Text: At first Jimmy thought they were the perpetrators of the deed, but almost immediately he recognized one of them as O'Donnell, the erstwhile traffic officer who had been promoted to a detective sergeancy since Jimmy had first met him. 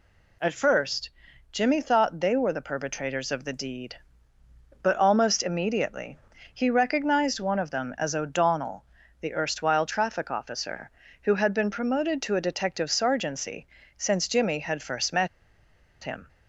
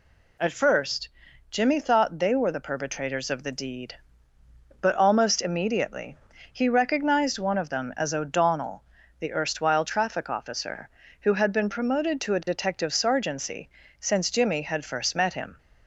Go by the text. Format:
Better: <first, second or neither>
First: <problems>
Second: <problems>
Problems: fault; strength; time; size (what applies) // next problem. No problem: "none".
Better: second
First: pauses between "first" and "Jimmy"; at 1.0 s; 0.42 s long // pauses between "immediately" and "he"; at 6.1 s; 0.38 s long // pauses between "sergeancy" and "since"; slight; at 13.6 s; 0.30 s long // pauses between "met" and "him"; noticeable; at 15.2 s; 0.75 s long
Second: pauses between "first" and "Jimmy"; at 1.0 s; 0.42 s long // pauses between "immediately" and "he"; at 6.1 s; 0.38 s long // pauses between "sergeancy" and "since"; slight; at 13.6 s; 0.30 s long